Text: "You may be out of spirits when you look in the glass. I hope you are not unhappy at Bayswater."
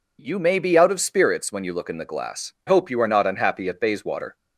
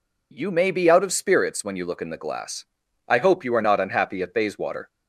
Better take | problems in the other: second | skips "I"; at 2.5 s

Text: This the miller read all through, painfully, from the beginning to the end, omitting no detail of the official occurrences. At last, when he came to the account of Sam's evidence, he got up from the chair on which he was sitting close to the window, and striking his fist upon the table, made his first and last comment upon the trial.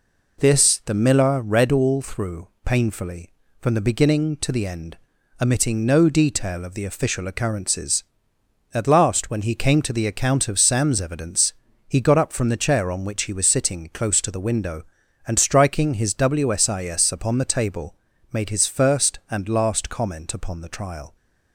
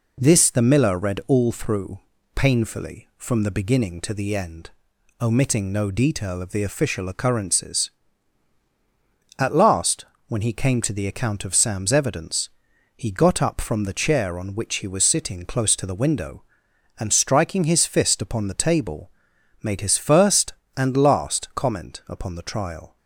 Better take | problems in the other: second | says "wsis" for "fist"; at 16.1 s

